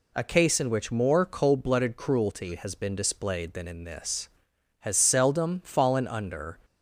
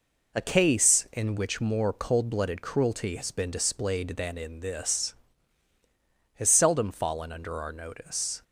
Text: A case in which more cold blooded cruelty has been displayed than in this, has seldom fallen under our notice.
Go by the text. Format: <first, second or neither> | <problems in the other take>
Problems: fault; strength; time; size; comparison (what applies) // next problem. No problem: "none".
second | stops before "our notice"; at 6.6 s